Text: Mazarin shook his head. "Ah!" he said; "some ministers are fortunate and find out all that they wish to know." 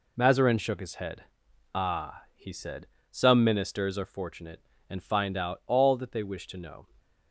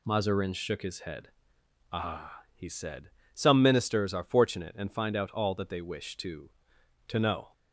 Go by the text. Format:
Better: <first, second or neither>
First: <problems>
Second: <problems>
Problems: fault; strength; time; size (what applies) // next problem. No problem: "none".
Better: first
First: none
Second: says "to" twice; at 7.0 s